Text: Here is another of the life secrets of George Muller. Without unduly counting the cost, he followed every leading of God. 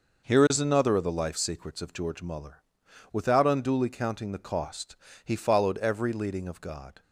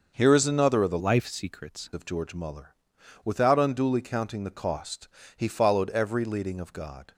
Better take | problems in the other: first | starts louder than the rest; until 1.1 s; 6.5 dB // changes voice from "life" to "secrets"; from 0.9 to 1.9 s; 1.0 s long

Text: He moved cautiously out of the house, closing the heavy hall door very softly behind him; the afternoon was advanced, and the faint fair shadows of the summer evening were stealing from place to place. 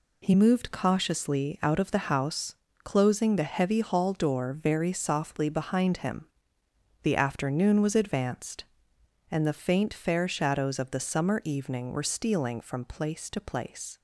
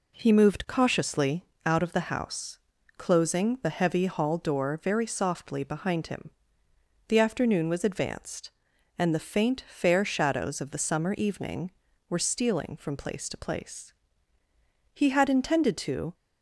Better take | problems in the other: first | pauses between "cautiously" and "out"; slight; at 1.4 s; 0.20 s long // goes on to say "He had intended to"; noticeable; from 14.9 s on; 1.2 s long

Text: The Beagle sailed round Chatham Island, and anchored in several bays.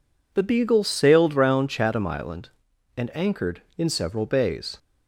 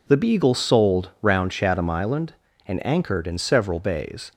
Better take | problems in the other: first | says "sold" for "sailed"; at 0.5 s

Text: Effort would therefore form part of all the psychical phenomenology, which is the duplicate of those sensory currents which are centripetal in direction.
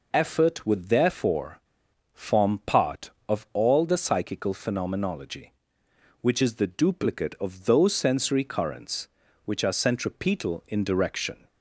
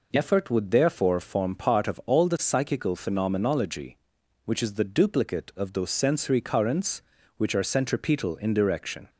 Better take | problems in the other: second | pauses between "therefore" and "form"; noticeable; at 1.6 s; 0.51 s long

